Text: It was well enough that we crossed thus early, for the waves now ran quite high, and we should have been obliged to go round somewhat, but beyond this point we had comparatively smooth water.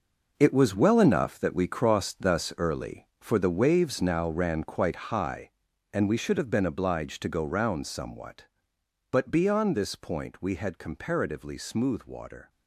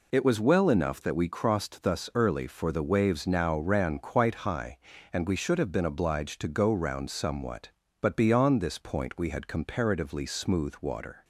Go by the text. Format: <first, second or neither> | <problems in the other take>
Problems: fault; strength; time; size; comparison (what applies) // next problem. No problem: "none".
second | gets quieter; strong; throughout; 10.5 dB